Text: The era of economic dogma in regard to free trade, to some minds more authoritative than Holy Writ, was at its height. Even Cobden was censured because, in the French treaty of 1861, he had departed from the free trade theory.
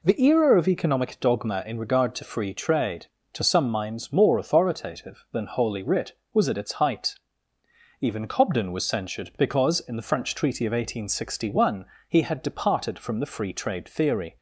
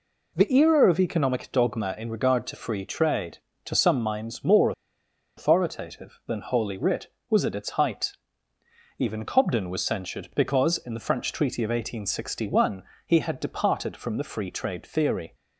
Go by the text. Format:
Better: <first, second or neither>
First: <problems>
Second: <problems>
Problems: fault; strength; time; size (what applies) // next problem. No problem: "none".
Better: first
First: none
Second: pauses between "more" and "authoritative"; noticeable; at 4.7 s; 0.65 s long